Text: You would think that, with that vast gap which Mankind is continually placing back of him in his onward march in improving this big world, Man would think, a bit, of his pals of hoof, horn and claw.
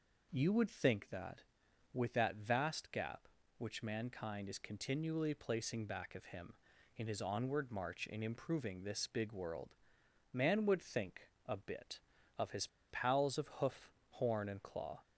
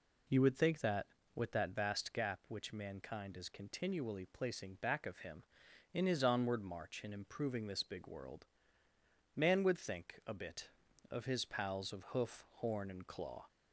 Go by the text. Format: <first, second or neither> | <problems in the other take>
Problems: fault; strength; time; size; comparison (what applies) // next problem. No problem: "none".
second | pauses between "his" and "pals"; slight; at 12.6 s; 0.22 s long